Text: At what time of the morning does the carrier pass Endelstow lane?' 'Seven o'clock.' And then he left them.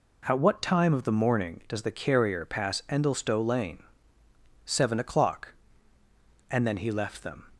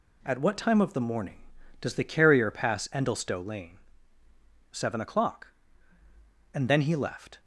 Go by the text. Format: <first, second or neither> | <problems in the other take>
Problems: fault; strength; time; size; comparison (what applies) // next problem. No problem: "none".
first | stops before "them"; at 7.3 s